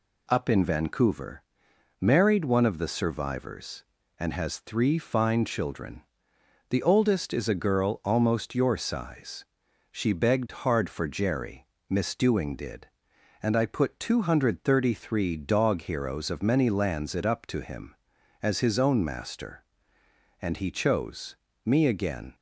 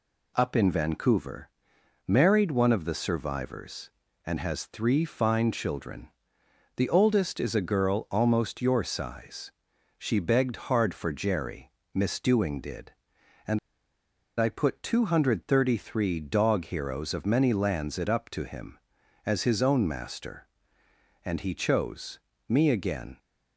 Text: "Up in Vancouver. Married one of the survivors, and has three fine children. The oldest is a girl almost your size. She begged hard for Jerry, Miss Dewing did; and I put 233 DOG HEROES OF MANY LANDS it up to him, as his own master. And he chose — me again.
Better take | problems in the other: first | pauses between "and" and "I"; noticeable; at 13.5 s; 0.81 s long

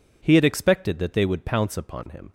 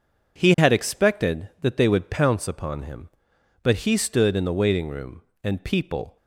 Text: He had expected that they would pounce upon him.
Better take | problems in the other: first | goes on to say "But he stood in the waiting room and people"; strong; from 3.6 s on; 2.5 s long

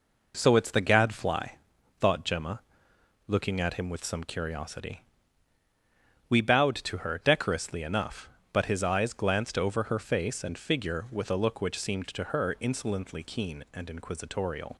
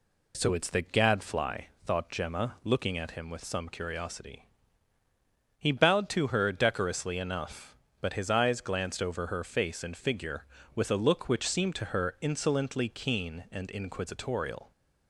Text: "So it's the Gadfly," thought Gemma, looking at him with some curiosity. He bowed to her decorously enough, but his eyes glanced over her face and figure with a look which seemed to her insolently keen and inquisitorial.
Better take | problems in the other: second | says "We" for "He"; at 6.2 s

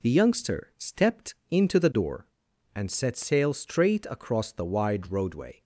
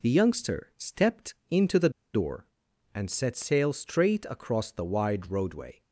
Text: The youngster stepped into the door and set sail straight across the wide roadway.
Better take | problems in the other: first | pauses between "stepped" and "into"; slight; at 1.3 s; 0.16 s long; slight in the first // pauses between "the" and "door"; slight; at 1.9 s; 0.23 s long

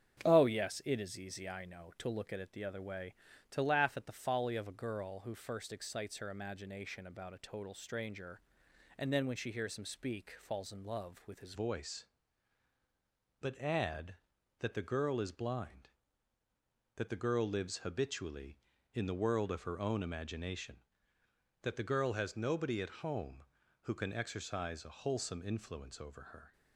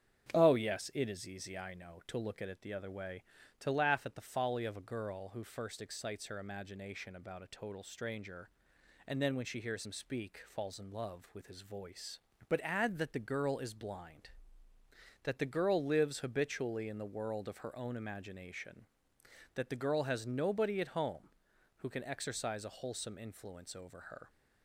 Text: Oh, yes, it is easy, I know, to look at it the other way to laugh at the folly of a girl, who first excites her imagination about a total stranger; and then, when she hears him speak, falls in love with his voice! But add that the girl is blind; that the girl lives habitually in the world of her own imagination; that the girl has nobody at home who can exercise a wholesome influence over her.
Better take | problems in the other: second | starts louder than the rest; strong; until 1.2 s; 8 dB; strong in the second // changes voice at "voice"; from 11.5 s on; 15.0 s long

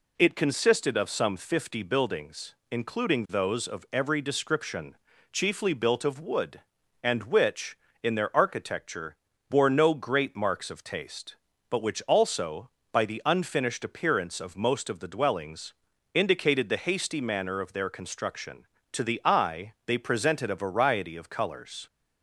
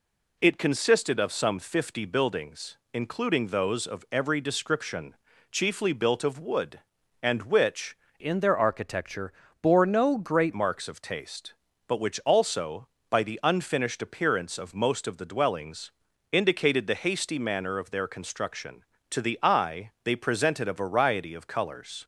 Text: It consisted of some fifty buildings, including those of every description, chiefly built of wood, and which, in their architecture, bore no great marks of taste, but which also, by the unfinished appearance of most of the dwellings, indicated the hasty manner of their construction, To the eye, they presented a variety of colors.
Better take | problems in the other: first | changes voice from "in" to "great"; from 8.1 to 10.5 s; 2.4 s long

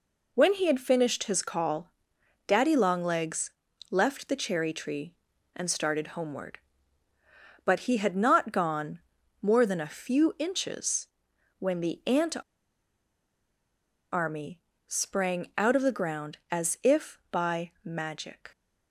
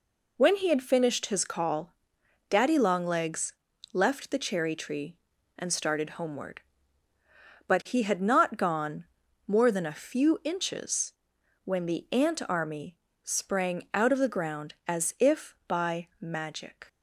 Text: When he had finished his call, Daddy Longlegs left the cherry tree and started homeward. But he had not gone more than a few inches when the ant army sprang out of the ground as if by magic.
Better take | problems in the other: second | pauses between "Longlegs" and "left"; at 3.5 s; 0.40 s long; also in the second // pauses between "gone" and "more"; at 9.0 s; 0.42 s long; also in the second // pauses between "inches" and "when"; noticeable; at 11.0 s; 0.52 s long; noticeable in the second // pauses between "ant" and "army"; strong; at 12.3 s; 1.7 s long // pauses between "army" and "sprang"; slight; at 14.5 s; 0.28 s long; slight in the second

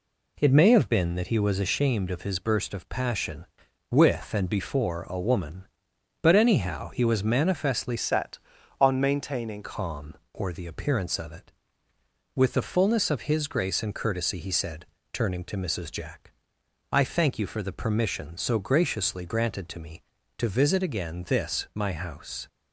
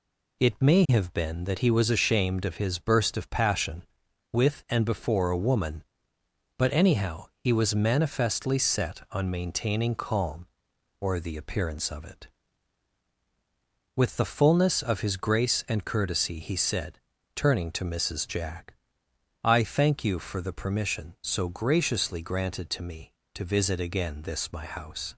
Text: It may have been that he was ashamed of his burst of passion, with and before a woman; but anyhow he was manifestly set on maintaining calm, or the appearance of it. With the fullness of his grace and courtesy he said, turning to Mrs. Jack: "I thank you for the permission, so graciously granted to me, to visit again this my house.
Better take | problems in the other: second | changes voice from "set" to "maintaining"; from 7.9 to 9.6 s; 1.7 s long

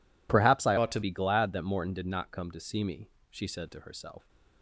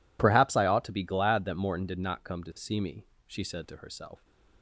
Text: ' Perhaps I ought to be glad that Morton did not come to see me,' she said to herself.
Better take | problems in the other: second | changes voice from "ought" to "to"; from 0.7 to 1.0 s; 0.3 s long

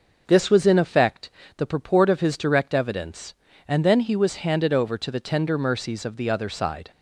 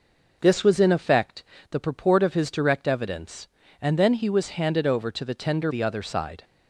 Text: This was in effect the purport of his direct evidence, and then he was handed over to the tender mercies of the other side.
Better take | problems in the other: first | pauses between "effect" and "the"; slight; at 1.4 s; 0.28 s long; slight in the first // skips "mercies of"; at 5.7 s

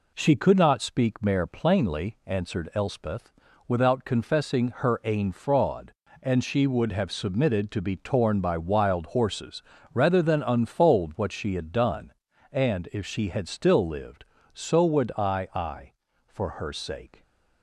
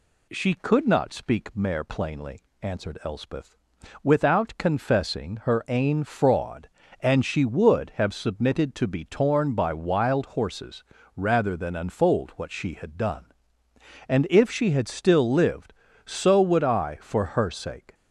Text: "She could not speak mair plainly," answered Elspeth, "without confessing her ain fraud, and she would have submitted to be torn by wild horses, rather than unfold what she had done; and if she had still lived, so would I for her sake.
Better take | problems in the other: second | says "I" twice; at 15.5 s

